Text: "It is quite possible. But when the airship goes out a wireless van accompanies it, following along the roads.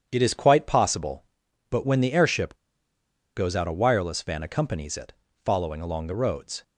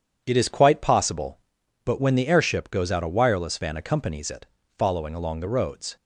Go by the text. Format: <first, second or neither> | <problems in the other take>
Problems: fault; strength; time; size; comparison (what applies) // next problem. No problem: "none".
second | pauses between "airship" and "goes"; noticeable; at 2.5 s; 0.79 s long